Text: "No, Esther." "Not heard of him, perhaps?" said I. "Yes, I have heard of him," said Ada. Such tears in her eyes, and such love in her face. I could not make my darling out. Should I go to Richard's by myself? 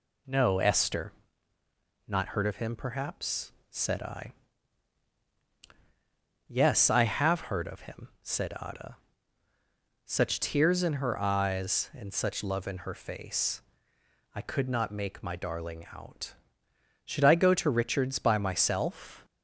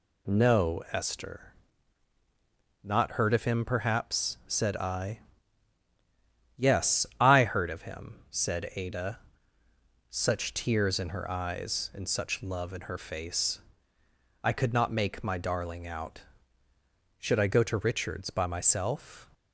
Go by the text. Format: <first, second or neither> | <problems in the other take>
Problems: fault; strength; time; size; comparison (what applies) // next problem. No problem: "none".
first | skips "have"; at 7.4 s